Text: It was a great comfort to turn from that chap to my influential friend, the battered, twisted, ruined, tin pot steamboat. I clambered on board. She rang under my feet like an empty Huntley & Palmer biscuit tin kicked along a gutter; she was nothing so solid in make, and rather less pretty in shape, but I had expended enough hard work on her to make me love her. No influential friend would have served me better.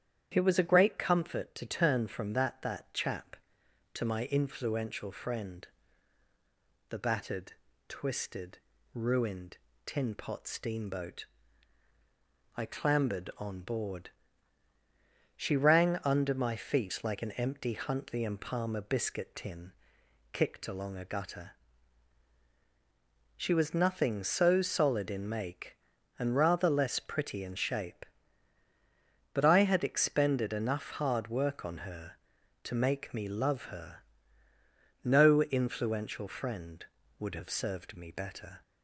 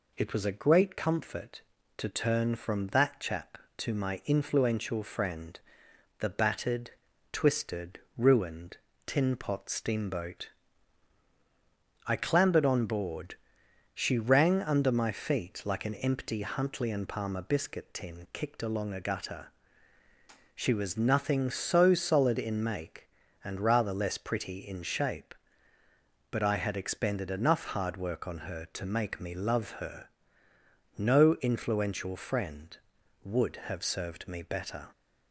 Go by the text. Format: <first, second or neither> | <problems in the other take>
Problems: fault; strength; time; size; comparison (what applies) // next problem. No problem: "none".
second | starts louder than the rest; strong; until 1.3 s; 9.5 dB // says "that" twice; at 2.6 s // pauses between "tin" and "kicked"; noticeable; at 19.7 s; 0.59 s long